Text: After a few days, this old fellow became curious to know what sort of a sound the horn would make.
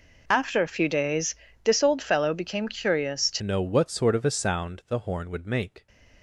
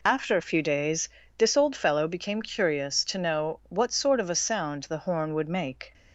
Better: second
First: changes voice at "know"; from 3.4 s on; 2.4 s long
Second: none

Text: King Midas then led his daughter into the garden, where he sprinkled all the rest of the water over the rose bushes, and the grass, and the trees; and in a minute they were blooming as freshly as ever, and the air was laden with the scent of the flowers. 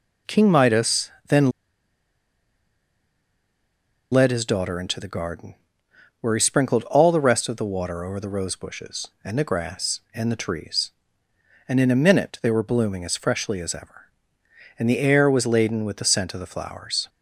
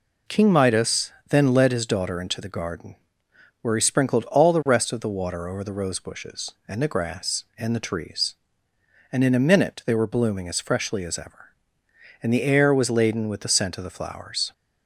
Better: second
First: pauses between "Midas" and "then"; slight; at 1.1 s; 0.18 s long // pauses between "then" and "led"; strong; at 1.5 s; 2.6 s long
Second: pauses between "Midas" and "then"; slight; at 1.1 s; 0.18 s long

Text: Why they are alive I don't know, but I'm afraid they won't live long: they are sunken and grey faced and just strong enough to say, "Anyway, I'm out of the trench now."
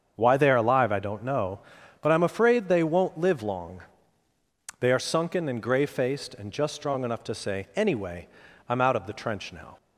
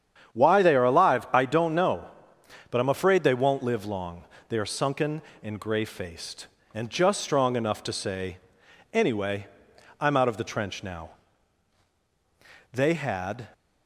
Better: first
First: starts louder than the rest; until 1.1 s; 7 dB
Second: starts louder than the rest; strong; until 1.3 s; 9 dB // goes on to say "They had"; noticeable; from 12.7 s on; 0.74 s long

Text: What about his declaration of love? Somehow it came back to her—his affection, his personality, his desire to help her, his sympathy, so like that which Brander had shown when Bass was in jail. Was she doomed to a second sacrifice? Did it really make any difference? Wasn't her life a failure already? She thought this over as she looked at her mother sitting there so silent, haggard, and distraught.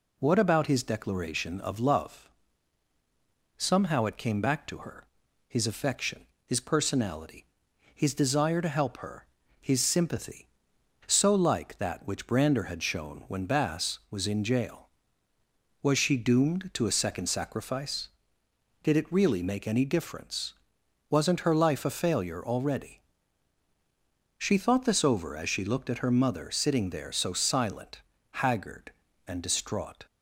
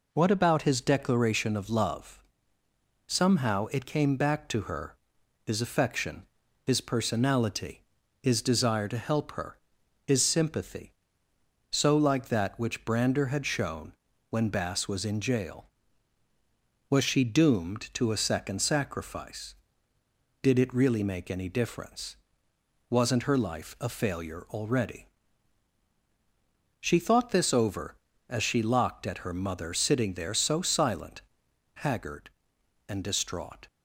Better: first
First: none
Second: pauses between "shown" and "when"; at 13.9 s; 0.38 s long // says "locked" for "looked"; at 28.6 s

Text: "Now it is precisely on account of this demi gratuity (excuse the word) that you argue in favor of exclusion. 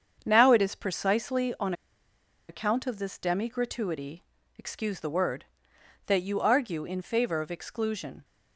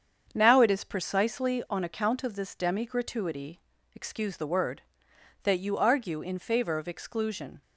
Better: second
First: starts louder than the rest; strong; until 1.2 s; 7 dB // pauses between "on" and "account"; noticeable; at 1.7 s; 0.76 s long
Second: starts louder than the rest; strong; until 1.3 s; 7 dB

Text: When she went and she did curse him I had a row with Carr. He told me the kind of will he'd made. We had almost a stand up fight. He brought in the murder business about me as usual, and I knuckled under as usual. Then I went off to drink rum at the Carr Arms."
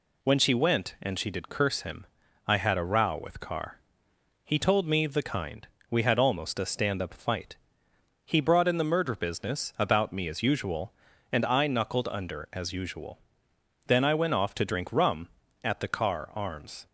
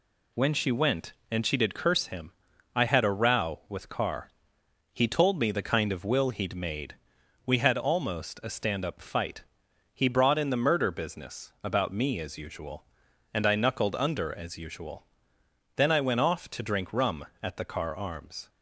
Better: second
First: pauses between "him" and "I"; at 2.0 s; 0.42 s long // skips "of will he'd made"; at 5.7 s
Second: pauses between "him" and "I"; at 2.3 s; 0.44 s long

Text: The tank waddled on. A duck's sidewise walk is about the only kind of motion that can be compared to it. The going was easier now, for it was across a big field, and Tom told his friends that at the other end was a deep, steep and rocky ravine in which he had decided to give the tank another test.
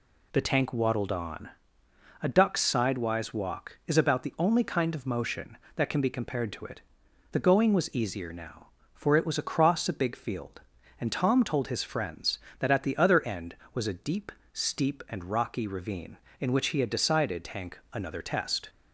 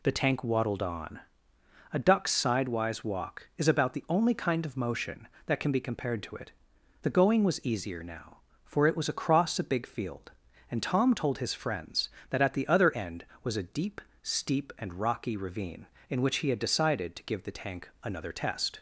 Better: second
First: skips "to give the"; at 17.4 s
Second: none

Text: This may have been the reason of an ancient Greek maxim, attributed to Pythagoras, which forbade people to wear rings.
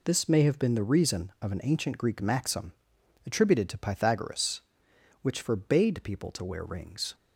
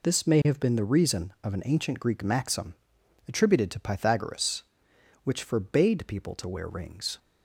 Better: neither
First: none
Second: none

